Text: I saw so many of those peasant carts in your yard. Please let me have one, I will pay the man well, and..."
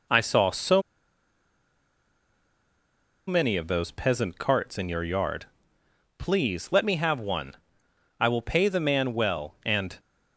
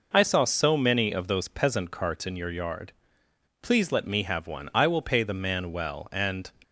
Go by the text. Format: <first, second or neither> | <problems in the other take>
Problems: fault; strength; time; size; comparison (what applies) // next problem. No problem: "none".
second | pauses between "so" and "many"; strong; at 0.8 s; 2.4 s long